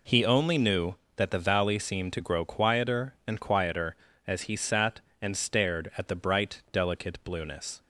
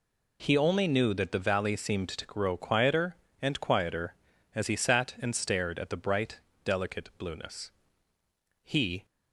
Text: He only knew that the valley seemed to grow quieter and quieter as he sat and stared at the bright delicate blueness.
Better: first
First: none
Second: pauses between "bright" and "delicate"; slight; at 6.3 s; 0.26 s long // goes on to say "He"; slight; from 8.6 s on; 0.42 s long

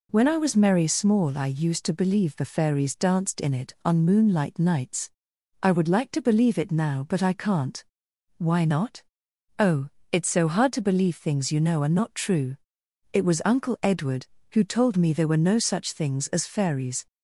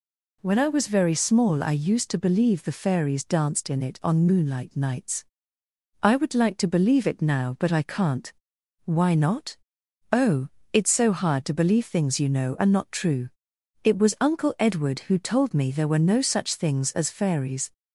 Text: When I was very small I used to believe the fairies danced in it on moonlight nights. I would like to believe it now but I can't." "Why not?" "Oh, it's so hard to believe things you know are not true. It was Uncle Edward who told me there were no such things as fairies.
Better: second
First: says "merry" for "very"; at 0.5 s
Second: none

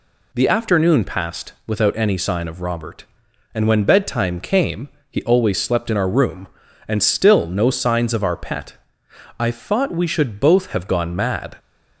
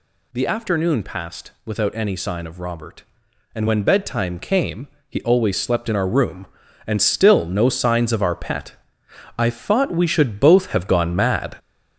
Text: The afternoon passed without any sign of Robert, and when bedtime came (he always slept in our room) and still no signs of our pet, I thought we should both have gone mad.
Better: first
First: none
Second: gets louder; noticeable; throughout; 5.5 dB

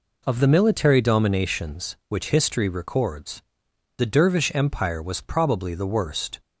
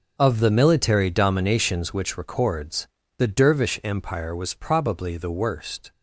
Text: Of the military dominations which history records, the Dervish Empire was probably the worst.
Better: first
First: none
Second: starts louder than the rest; until 1.1 s; 6 dB // skips "history"; at 2.1 s

